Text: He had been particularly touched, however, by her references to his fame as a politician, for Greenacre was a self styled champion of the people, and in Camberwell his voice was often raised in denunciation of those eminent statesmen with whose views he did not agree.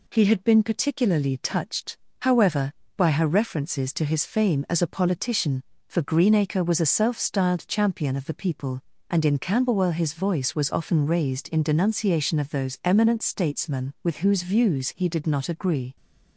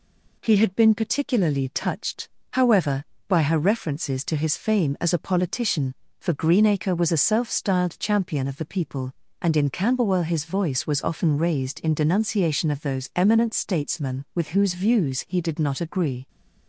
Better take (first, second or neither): neither